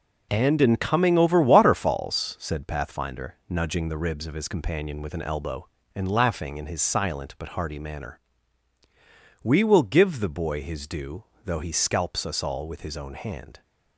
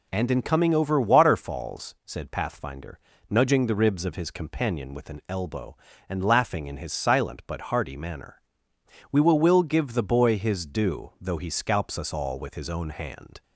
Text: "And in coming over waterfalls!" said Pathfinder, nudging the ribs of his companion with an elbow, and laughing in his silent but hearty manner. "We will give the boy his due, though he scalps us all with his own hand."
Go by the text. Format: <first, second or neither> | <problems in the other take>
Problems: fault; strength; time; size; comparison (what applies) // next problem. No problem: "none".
first | says "will" twice; at 9.3 s